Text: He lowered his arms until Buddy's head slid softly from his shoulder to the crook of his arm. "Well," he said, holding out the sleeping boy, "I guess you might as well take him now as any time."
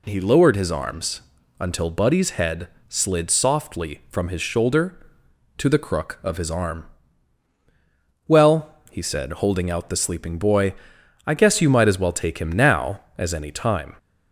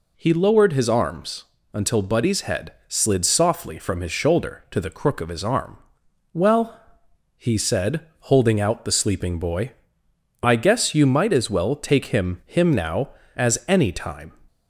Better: first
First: pauses between "arms" and "until"; at 1.2 s; 0.38 s long // pauses between "head" and "slid"; slight; at 2.6 s; 0.20 s long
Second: pauses between "arms" and "until"; slight; at 1.4 s; 0.30 s long // pauses between "head" and "slid"; slight; at 2.7 s; 0.16 s long // says "him" twice; at 12.4 s

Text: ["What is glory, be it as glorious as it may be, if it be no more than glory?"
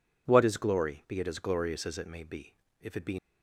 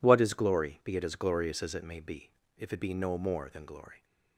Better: second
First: stops before "no more than glory"; at 3.1 s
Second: none

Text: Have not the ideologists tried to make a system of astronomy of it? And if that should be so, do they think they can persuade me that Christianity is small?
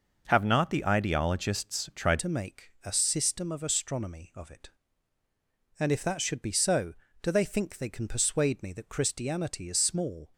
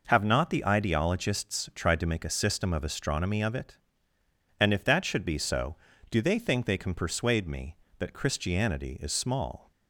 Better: second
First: changes voice at "to"; from 2.1 s on; 8.2 s long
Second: none

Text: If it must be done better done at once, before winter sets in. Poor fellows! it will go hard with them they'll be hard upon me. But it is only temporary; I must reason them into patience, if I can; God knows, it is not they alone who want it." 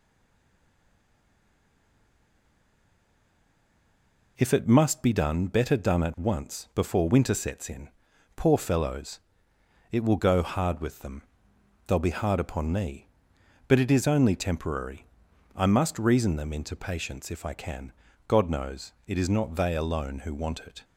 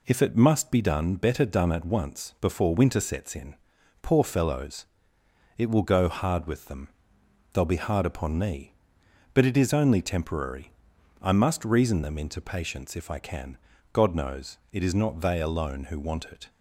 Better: second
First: stays silent before the first word; strong; until 4.3 s; 4.3 s long // pauses between "them" and "they'll"; noticeable; at 11.2 s; 0.64 s long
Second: pauses between "them" and "they'll"; noticeable; at 6.8 s; 0.64 s long

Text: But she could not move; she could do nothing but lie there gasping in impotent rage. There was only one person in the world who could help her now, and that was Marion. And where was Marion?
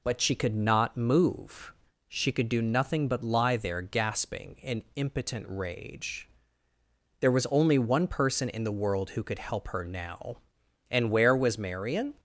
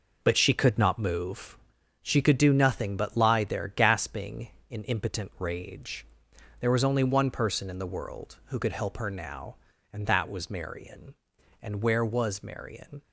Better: second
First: skips "and that was Marion"; at 10.6 s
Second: none

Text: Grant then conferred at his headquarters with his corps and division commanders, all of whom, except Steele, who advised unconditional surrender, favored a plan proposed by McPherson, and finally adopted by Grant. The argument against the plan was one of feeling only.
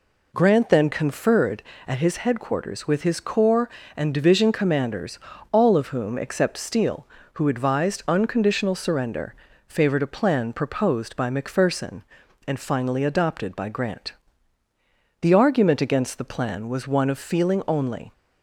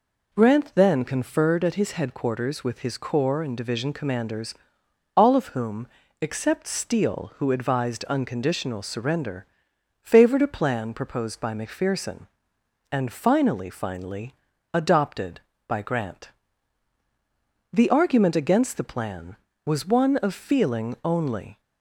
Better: first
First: none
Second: says "finally" twice; at 13.6 s

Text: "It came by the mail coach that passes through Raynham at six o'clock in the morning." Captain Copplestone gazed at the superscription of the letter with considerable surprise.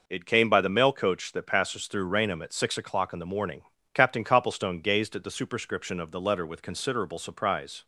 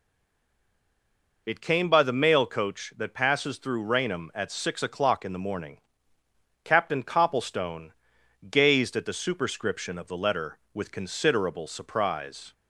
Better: first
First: none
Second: stays silent before the first word; noticeable; until 1.4 s; 1.4 s long // pauses between "Copplestone" and "gazed"; noticeable; at 7.9 s; 0.56 s long

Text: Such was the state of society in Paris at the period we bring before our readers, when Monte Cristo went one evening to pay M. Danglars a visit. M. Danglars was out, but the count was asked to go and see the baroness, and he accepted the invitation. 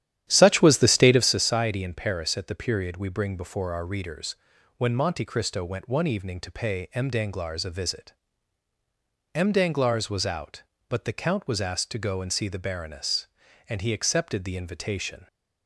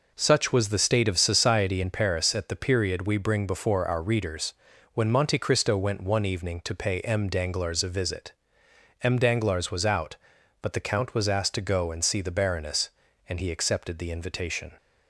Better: second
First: starts louder than the rest; strong; until 1.4 s; 11 dB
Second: none

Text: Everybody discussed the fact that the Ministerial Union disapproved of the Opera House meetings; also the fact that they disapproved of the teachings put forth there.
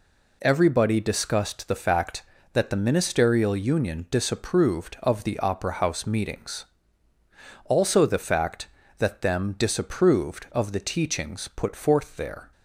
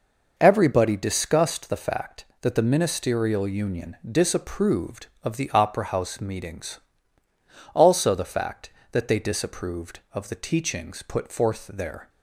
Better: second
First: says "them" for "they"; at 9.1 s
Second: none

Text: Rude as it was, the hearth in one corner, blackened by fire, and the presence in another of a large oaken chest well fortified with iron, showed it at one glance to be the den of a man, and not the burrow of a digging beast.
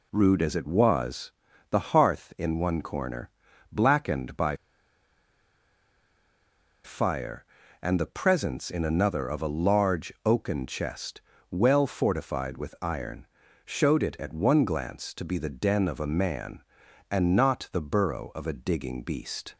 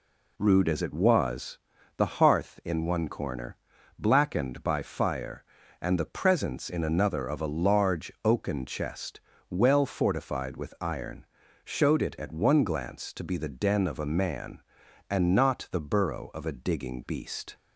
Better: second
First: pauses between "by" and "fire"; strong; at 4.5 s; 2.2 s long // pauses between "chest" and "well"; slight; at 11.2 s; 0.28 s long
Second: pauses between "chest" and "well"; slight; at 9.1 s; 0.28 s long

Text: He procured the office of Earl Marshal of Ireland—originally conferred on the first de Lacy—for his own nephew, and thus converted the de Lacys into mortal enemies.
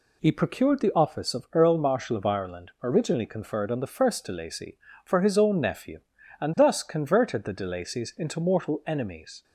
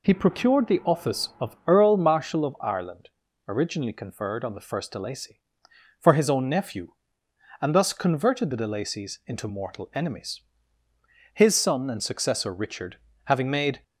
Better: first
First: none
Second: goes on to say "His son and successor Richard having made"; strong; from 11.3 s on; 2.5 s long

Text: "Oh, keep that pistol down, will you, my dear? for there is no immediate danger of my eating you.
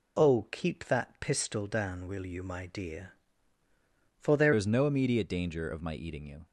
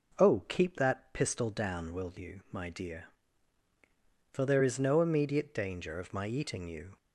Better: second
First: changes voice at "is"; from 4.5 s on; 1.9 s long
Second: none

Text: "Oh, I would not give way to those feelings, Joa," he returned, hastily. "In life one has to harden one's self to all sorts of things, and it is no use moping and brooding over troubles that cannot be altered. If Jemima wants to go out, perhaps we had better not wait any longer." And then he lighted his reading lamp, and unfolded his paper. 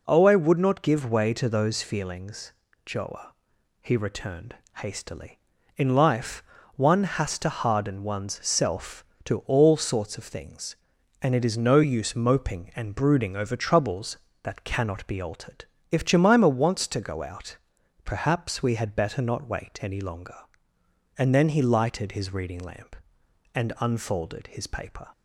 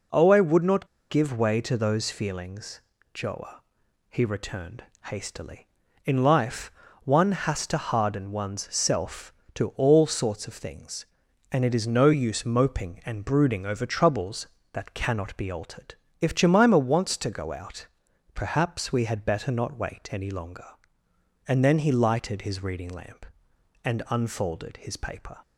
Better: first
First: pauses between "life" and "one"; slight; at 6.4 s; 0.34 s long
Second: pauses between "not" and "give"; slight; at 0.8 s; 0.22 s long // pauses between "life" and "one"; slight; at 6.6 s; 0.34 s long

